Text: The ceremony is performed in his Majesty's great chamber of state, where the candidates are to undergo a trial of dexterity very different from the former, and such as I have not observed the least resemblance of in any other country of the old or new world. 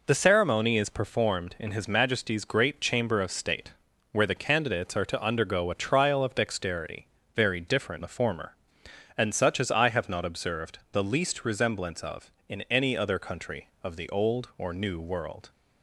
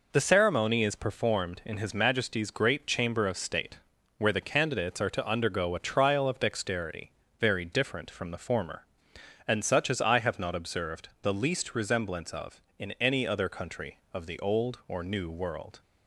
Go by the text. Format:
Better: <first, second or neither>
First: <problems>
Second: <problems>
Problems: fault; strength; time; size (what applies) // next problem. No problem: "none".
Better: second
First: pauses between "dexterity" and "very"; slight; at 7.0 s; 0.30 s long // skips "from"; at 8.0 s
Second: pauses between "dexterity" and "very"; slight; at 7.1 s; 0.30 s long